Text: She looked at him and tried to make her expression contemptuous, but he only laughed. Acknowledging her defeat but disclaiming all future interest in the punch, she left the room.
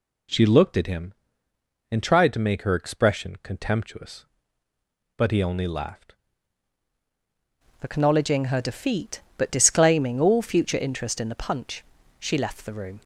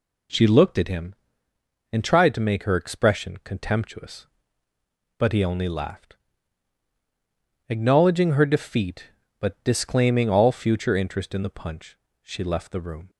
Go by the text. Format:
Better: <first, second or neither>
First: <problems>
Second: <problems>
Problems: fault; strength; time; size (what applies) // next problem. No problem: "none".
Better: second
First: changes voice at "Acknowledging"; from 7.8 s on; 5.2 s long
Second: none